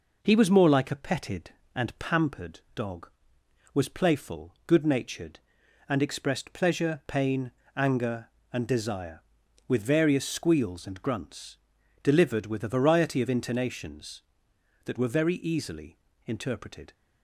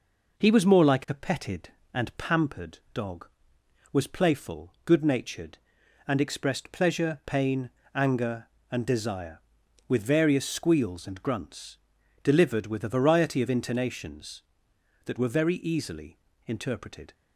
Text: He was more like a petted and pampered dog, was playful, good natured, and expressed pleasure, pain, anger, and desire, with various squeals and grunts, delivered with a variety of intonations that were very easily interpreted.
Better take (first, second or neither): neither